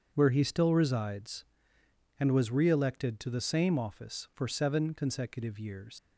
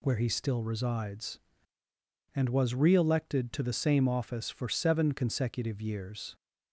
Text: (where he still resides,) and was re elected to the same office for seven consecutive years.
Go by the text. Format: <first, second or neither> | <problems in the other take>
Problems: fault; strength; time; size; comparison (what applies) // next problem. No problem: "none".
second | starts louder than the rest; until 1.1 s; 7 dB // leaves "years" unfinished; at 5.9 s; 125 ms